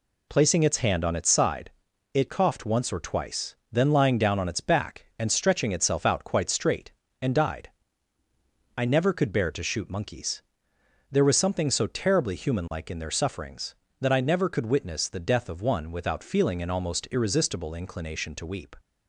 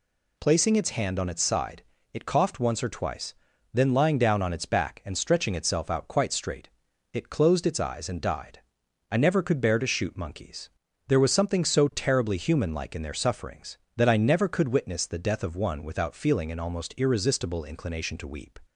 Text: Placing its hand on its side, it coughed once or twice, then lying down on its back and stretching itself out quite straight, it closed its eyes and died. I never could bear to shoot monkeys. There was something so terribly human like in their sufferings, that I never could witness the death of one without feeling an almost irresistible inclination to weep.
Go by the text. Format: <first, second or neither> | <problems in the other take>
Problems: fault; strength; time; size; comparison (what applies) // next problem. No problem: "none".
second | skips "it closed its eyes"; at 7.0 s